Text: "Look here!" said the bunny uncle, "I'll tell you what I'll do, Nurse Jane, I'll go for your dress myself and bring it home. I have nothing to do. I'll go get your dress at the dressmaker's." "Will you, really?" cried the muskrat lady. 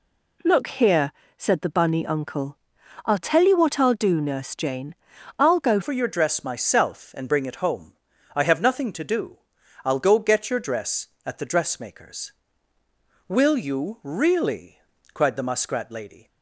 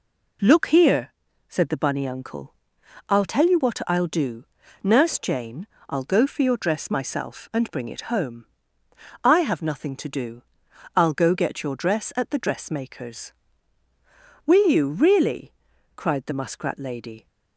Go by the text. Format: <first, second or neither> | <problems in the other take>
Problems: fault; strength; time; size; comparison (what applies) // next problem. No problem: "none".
second | changes voice at "for"; from 5.8 s on; 10.4 s long